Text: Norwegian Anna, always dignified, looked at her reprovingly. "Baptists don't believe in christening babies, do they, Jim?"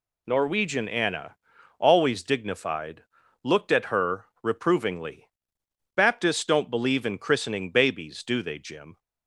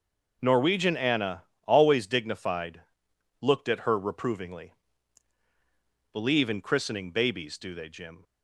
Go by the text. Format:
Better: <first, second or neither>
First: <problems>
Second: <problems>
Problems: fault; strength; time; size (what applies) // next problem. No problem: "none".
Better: first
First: none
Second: skips "Baptists don't"; at 5.4 s